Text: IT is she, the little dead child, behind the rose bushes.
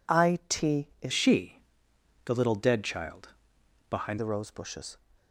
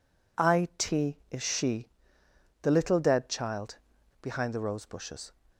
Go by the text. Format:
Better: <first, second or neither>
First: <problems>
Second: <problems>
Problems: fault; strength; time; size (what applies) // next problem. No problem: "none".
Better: second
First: changes voice from "she" to "behind"; from 1.1 to 4.1 s; 3.0 s long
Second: none